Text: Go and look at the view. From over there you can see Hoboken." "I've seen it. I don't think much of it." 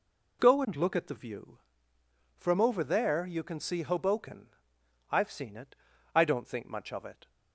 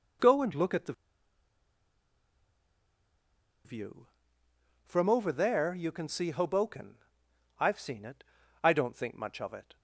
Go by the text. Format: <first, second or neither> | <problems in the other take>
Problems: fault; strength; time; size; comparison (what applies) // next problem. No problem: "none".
first | pauses between "the" and "view"; strong; at 0.9 s; 2.7 s long